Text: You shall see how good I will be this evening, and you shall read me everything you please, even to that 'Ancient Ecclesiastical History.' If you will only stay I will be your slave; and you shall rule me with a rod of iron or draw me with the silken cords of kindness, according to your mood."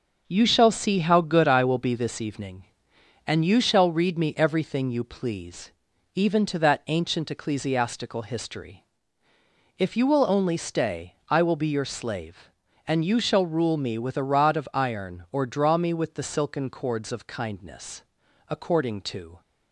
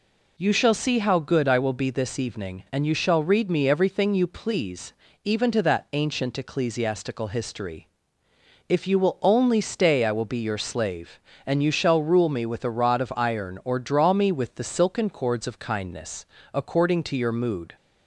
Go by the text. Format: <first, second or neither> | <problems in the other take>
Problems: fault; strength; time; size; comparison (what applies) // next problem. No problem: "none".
second | starts louder than the rest; until 1.2 s; 6.5 dB // pauses between "stay" and "I"; slight; at 11.1 s; 0.16 s long // stops before "your mood"; at 19.4 s